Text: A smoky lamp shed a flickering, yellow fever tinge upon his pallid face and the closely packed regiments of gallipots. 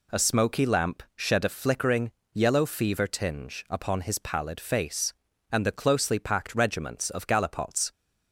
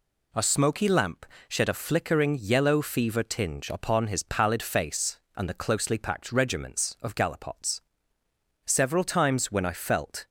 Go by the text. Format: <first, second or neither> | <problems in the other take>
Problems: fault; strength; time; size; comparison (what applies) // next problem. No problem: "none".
first | pauses between "lamp" and "shed"; slight; at 1.2 s; 0.24 s long // goes on to say "Several times when I felt"; from 8.6 s on; 1.6 s long